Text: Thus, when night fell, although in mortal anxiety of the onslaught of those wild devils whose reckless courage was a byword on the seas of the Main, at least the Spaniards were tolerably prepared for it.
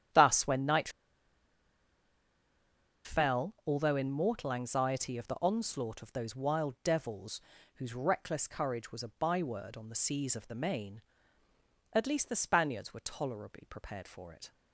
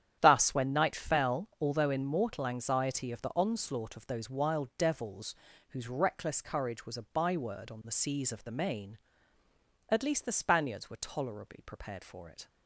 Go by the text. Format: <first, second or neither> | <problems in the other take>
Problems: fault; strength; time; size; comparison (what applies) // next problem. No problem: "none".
second | starts louder than the rest; strong; until 3.2 s; 10.5 dB; strong in the second // pauses between "night" and "fell"; strong; at 0.8 s; 2.1 s long // pauses between "devils" and "whose"; slight; at 7.4 s; 0.32 s long; slight in the second